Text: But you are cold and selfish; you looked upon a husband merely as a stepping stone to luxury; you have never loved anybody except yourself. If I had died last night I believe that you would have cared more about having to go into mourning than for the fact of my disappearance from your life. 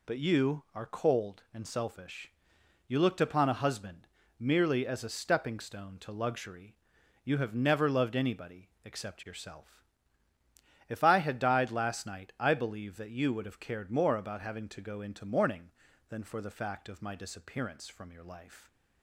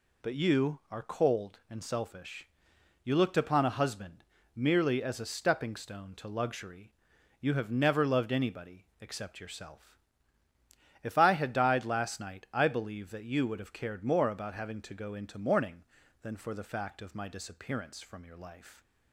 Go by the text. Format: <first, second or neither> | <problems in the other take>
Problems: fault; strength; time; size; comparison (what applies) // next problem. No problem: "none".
neither | pauses between "husband" and "merely"; slight; the same in both // pauses between "anybody" and "except"; slight; the same in both